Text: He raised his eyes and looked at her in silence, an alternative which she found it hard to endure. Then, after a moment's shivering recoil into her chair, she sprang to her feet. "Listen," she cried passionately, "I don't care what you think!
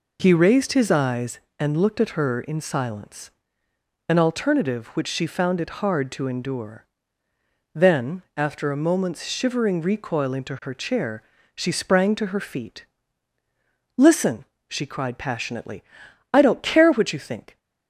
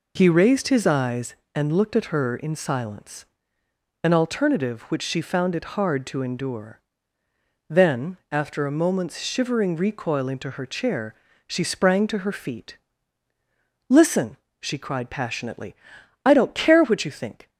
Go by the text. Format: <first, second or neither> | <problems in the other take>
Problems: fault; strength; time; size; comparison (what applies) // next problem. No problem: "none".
neither | none